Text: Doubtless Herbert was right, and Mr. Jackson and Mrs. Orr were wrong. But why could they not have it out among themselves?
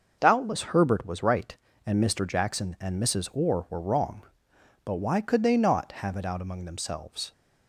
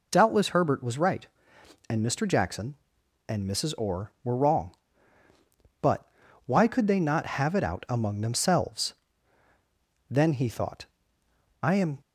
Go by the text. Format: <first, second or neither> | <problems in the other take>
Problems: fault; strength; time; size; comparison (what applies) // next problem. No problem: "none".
first | pauses between "But" and "why"; at 6.0 s; 0.38 s long // goes on to say "Then he thought I am"; strong; from 10.1 s on; 1.8 s long